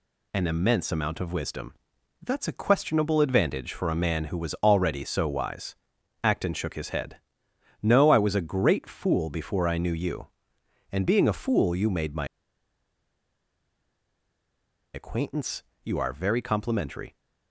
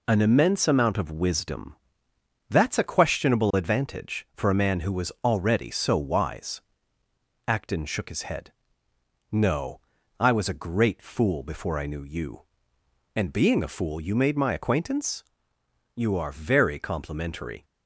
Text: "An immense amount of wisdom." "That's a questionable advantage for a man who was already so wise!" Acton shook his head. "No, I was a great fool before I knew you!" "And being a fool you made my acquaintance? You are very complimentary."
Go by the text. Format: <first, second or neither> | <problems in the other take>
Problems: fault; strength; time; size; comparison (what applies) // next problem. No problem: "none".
second | pauses between "my" and "acquaintance"; strong; at 12.2 s; 2.6 s long